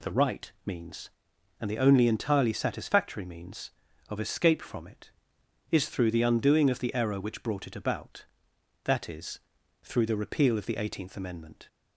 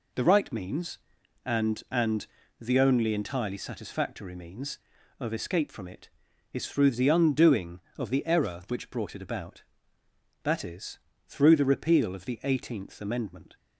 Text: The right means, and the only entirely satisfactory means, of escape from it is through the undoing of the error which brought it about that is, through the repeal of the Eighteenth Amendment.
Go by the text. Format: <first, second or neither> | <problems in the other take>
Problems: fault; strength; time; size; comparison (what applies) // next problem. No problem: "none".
first | says "and" twice; at 1.8 s